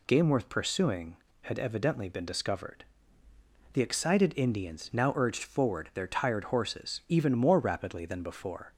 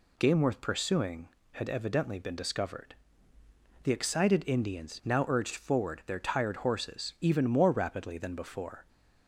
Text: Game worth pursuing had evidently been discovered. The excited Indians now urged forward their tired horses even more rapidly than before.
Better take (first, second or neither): neither